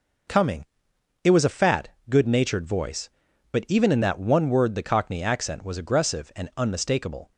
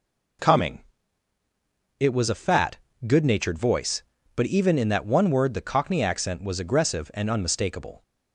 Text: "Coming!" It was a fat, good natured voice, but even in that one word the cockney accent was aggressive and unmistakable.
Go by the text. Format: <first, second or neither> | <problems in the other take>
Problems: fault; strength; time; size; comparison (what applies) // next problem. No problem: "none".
neither | none